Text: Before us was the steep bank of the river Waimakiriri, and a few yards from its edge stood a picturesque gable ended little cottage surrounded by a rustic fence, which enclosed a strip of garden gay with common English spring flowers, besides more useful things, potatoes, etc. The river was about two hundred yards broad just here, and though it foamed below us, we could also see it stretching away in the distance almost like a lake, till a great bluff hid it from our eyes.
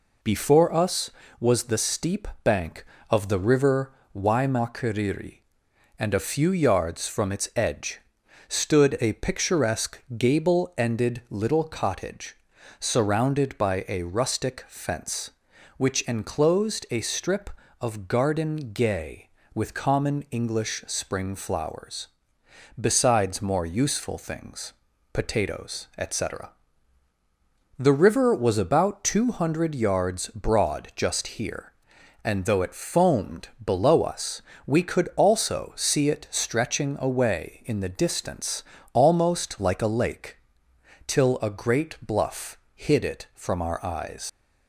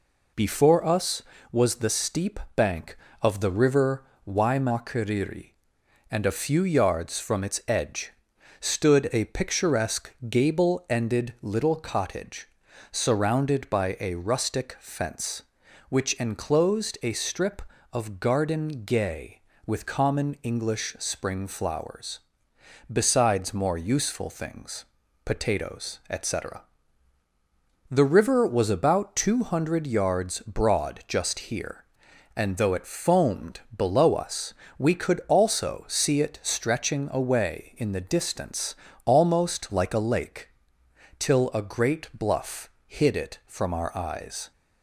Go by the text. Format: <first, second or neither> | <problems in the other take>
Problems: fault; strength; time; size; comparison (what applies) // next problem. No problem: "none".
second | pauses between "steep" and "bank"; slight; at 2.2 s; 0.16 s long; slight in the second // pauses between "river" and "Waimakiriri"; slight; at 3.9 s; 0.22 s long; slight in the second // pauses between "edge" and "stood"; noticeable; at 7.9 s; 0.50 s long; noticeable in the second // pauses between "picturesque" and "gable"; slight; at 10.0 s; 0.16 s long; slight in the second // pauses between "cottage" and "surrounded"; at 12.3 s; 0.42 s long; also in the second // pauses between "foamed" and "below"; slight; at 33.4 s; 0.16 s long; slight in the second // pauses between "distance" and "almost"; slight; at 38.6 s; 0.30 s long; slight in the second // pauses between "bluff" and "hid"; slight; at 42.5 s; 0.16 s long; slight in the second // leaves "eyes" unfinished; at 44.2 s; 100 ms